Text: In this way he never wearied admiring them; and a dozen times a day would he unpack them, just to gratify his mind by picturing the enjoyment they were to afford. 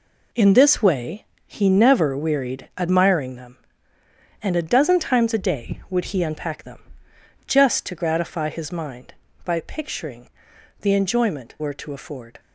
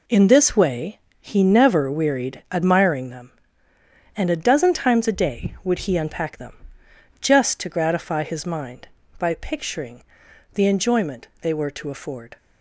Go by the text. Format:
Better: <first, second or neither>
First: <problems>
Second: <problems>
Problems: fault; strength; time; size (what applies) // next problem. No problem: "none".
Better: second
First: pauses between "way" and "he"; slight; at 1.2 s; 0.20 s long // pauses between "picturing" and "the"; noticeable; at 10.2 s; 0.50 s long // skips "they"; at 11.5 s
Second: pauses between "way" and "he"; slight; at 0.9 s; 0.20 s long // pauses between "picturing" and "the"; noticeable; at 10.0 s; 0.48 s long